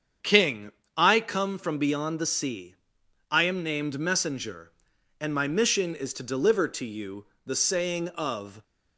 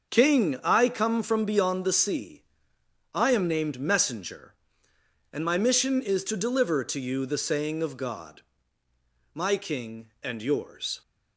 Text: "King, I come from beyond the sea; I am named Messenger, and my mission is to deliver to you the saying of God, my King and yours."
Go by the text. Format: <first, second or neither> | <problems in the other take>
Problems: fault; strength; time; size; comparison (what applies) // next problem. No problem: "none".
second | starts louder than the rest; strong; until 1.4 s; 7.5 dB; also in the second // pauses between "you" and "the"; slight; at 7.2 s; 0.22 s long // stops before "God my King and yours"; at 8.6 s